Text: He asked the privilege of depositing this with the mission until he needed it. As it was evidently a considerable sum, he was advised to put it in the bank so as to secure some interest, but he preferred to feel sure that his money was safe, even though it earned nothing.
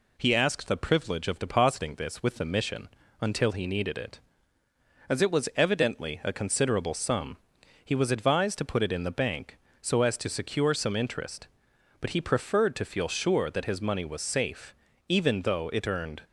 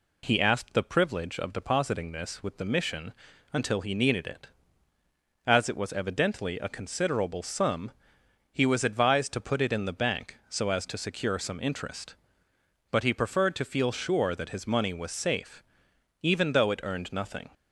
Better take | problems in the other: second | pauses between "mission" and "until"; slight; at 2.8 s; 0.32 s long; also in the second // stops before "nothing"; at 16.2 s

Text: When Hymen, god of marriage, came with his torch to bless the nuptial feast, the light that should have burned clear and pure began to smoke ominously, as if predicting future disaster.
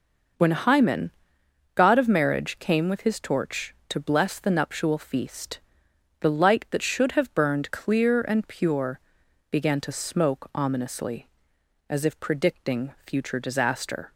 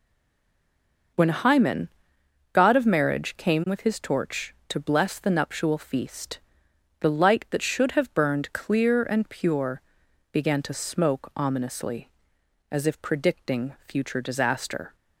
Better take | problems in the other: first | stays silent before the first word; until 1.1 s; 1.1 s long // pauses between "pure" and "began"; noticeable; at 9.8 s; 0.52 s long; noticeable in the first

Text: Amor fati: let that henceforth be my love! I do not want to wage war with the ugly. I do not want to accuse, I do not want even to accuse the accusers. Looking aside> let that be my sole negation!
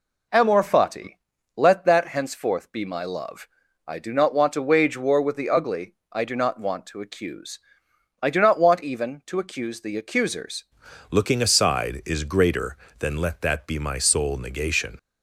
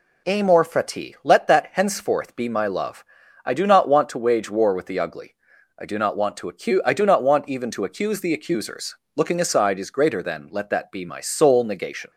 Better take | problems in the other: second | changes voice at "Looking"; from 11.1 s on; 3.8 s long

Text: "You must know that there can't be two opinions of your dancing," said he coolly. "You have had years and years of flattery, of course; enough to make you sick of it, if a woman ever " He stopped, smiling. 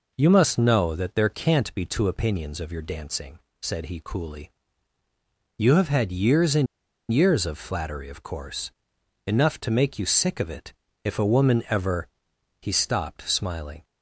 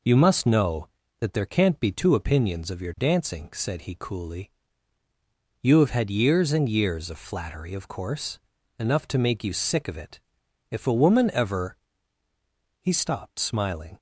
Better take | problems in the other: second | pauses between "and" and "years"; at 6.6 s; 0.45 s long

